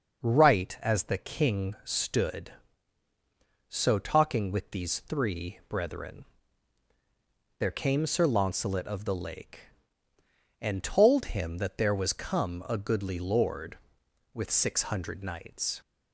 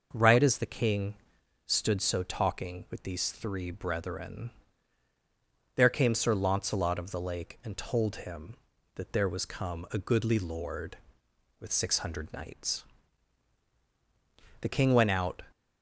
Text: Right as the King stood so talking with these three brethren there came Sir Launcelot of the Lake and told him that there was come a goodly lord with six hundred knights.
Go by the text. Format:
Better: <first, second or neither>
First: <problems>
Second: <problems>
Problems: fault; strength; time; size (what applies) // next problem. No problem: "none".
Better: first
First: pauses between "brethren" and "there"; strong; at 6.2 s; 1.3 s long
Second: pauses between "King" and "stood"; noticeable; at 1.1 s; 0.52 s long // pauses between "brethren" and "there"; strong; at 4.4 s; 1.2 s long // goes on to say "The King went out"; noticeable; from 14.5 s on; 0.86 s long